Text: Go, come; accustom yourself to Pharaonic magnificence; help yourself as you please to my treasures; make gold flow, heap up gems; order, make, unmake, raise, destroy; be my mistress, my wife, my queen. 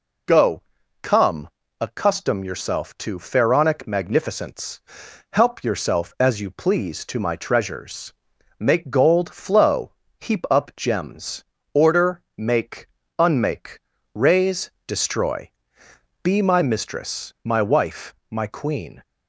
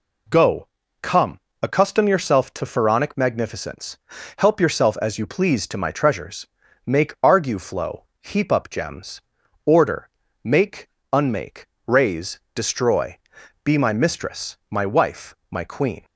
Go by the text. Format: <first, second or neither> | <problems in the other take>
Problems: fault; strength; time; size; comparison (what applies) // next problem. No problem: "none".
first | says "argue" for "gold"; at 7.2 s